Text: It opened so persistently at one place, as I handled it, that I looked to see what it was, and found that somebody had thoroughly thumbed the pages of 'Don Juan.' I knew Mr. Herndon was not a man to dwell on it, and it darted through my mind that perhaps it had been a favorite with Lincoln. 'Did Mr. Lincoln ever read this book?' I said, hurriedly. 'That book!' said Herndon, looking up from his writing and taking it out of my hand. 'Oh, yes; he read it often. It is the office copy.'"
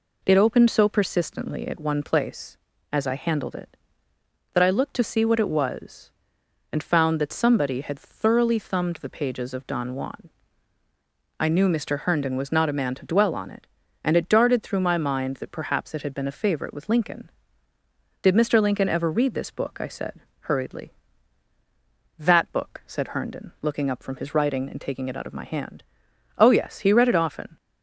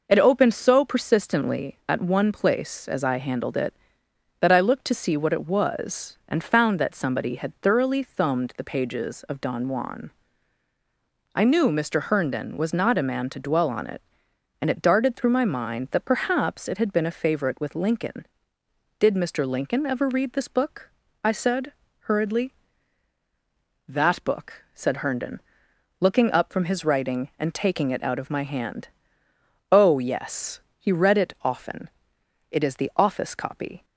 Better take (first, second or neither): second